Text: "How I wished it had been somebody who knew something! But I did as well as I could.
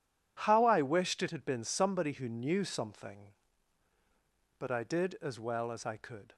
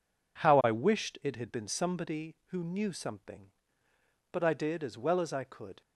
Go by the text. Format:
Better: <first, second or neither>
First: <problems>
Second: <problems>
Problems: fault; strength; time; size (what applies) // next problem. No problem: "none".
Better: neither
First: none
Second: none